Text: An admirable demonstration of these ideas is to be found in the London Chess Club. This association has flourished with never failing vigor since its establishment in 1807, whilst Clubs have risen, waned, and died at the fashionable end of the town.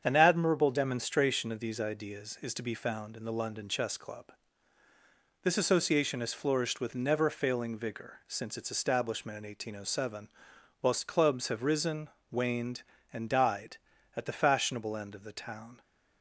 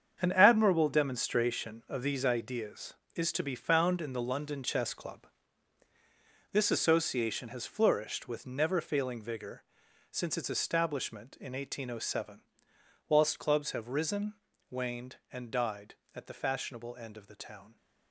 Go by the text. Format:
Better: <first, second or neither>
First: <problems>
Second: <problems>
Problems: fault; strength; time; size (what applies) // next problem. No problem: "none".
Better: first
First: starts louder than the rest; strong; until 1.0 s; 7.5 dB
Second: gets quieter; strong; throughout; 9.5 dB // starts louder than the rest; strong; until 1.2 s; 7.5 dB // pauses between "vigor" and "since"; noticeable; at 9.6 s; 0.48 s long